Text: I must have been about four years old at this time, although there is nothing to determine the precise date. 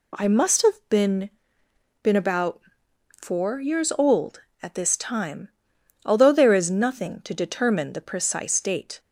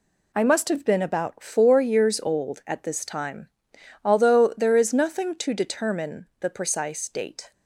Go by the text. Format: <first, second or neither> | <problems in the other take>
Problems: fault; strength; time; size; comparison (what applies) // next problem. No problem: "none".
second | says "been" twice; at 2.0 s // pauses between "about" and "four"; noticeable; at 2.5 s; 0.62 s long